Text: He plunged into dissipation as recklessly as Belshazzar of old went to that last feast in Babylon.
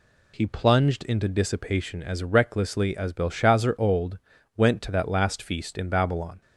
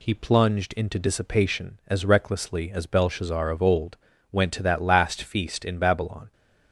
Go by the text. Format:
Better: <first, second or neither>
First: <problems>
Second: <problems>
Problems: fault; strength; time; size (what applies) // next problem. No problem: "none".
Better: second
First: skips "of"; at 3.7 s // pauses between "old" and "went"; at 4.1 s; 0.38 s long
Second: pauses between "old" and "went"; slight; at 3.9 s; 0.36 s long